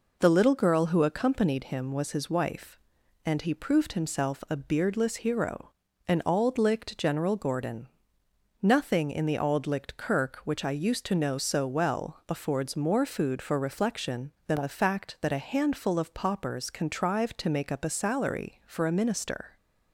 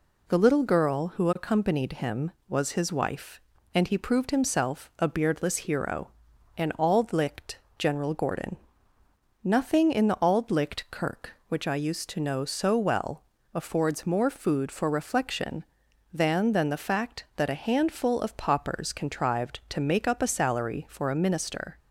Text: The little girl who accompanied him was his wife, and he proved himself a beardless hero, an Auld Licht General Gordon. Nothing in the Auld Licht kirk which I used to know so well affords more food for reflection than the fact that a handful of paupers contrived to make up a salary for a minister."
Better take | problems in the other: first | pauses between "Licht" and "General"; slight; at 7.5 s; 0.22 s long // pauses between "well" and "affords"; slight; at 13.2 s; 0.32 s long // says "than" twice; at 16.5 s

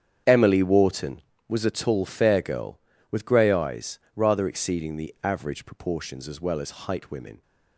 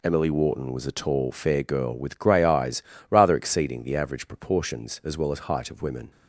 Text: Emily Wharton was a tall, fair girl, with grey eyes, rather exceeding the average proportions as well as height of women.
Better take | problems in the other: second | starts louder than the rest; strong; until 1.5 s; 8.5 dB // skips "of"; at 7.0 s

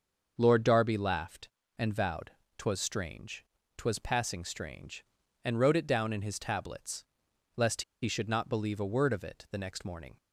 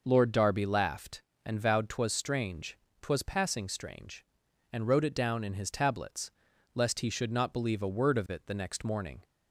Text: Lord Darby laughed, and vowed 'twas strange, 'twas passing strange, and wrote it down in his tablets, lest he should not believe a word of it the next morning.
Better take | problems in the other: second | starts louder than the rest; until 1.3 s; 6.5 dB // pauses between "vowed" and "twas"; slight; at 2.3 s; 0.26 s long // pauses between "lest" and "he"; slight; at 7.8 s; 0.19 s long

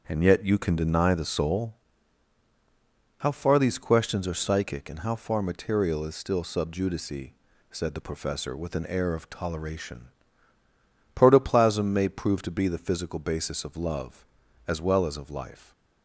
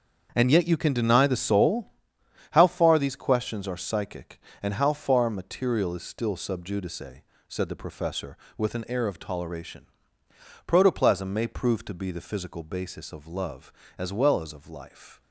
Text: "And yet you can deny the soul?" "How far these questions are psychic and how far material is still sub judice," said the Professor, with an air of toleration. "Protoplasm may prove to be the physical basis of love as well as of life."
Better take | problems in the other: neither | starts louder than the rest; the same in both

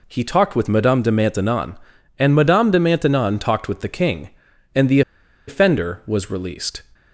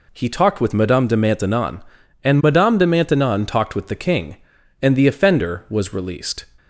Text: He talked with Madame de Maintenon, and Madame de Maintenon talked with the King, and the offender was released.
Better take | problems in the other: second | pauses between "the" and "offender"; noticeable; at 5.0 s; 0.47 s long

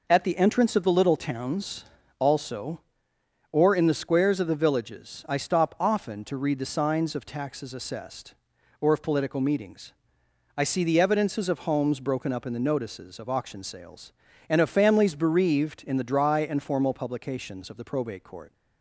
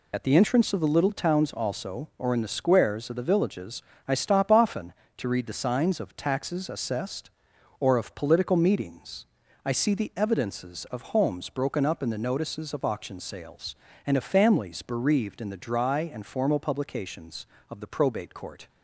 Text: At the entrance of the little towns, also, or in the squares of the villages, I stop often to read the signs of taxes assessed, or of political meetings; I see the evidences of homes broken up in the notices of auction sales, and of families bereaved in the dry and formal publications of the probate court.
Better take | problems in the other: first | loses the start of "At"; at 0.1 s; 45 ms

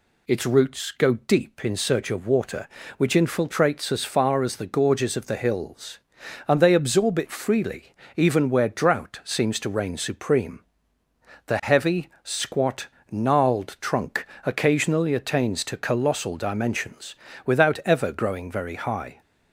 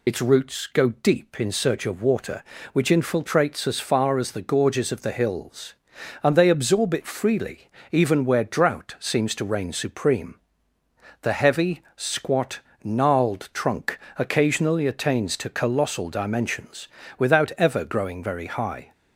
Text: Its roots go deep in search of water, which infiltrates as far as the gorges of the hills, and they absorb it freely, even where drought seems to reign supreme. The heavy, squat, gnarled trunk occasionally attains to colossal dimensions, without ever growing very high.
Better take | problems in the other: first | loses the start of "Its"; at 0.0 s; 40 ms // pauses between "trunk" and "occasionally"; slight; at 13.9 s; 0.18 s long; slight in the first

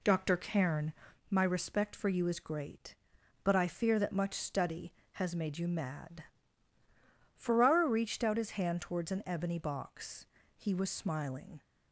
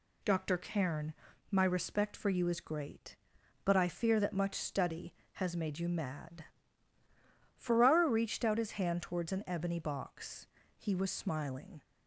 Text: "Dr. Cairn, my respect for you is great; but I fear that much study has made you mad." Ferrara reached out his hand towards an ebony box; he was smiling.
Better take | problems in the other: second | starts louder than the rest; slight; until 1.2 s; 2 dB

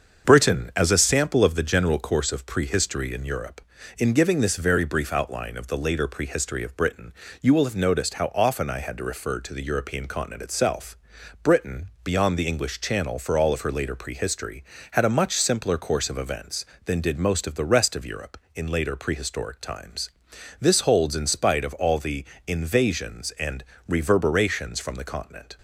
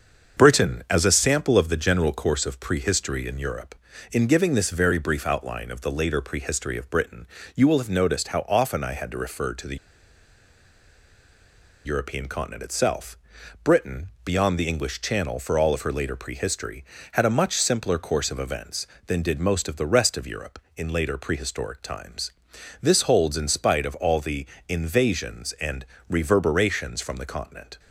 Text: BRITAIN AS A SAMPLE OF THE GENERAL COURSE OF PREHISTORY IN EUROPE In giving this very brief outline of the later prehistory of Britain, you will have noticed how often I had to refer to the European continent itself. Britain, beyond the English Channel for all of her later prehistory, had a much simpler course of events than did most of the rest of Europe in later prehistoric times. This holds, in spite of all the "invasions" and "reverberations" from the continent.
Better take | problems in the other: first | starts louder than the rest; until 1.4 s; 7 dB; also in the first // pauses between "the" and "European"; strong; at 9.7 s; 2.0 s long // pauses between "the" and "invasions"; slight; at 24.4 s; 0.24 s long; slight in the first // pauses between "and" and "reverberations"; slight; at 25.8 s; 0.24 s long; slight in the first

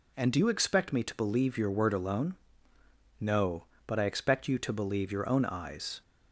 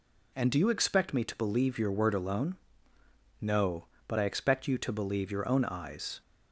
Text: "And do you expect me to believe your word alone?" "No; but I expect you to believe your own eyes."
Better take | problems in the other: neither | none

